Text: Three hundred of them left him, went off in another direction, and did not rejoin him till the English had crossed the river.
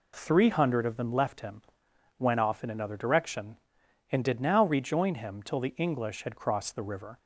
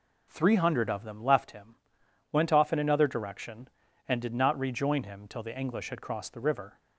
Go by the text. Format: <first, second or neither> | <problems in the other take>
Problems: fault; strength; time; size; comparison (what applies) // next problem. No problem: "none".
second | says "now" for "not"; at 4.3 s